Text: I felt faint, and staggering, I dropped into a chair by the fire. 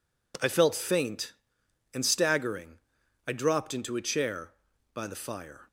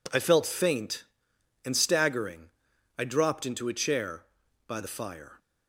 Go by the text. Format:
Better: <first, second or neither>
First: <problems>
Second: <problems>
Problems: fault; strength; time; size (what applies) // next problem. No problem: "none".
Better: neither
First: none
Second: none